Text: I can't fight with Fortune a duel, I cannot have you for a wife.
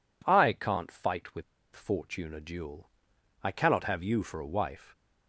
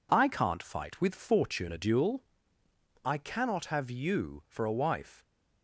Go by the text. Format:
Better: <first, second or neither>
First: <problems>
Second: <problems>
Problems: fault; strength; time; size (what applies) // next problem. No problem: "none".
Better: second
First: pauses between "with" and "Fortune"; slight; at 1.4 s; 0.31 s long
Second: none